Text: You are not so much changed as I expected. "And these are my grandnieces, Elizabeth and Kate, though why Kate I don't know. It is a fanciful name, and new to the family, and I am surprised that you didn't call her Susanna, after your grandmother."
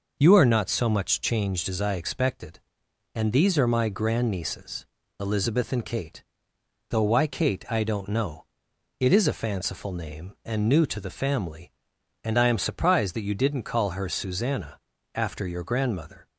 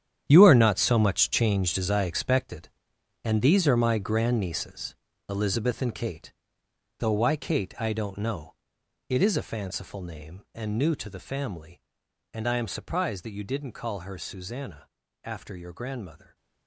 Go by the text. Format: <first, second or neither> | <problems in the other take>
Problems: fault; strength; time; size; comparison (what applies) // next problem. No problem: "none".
first | gets quieter; strong; throughout; 13 dB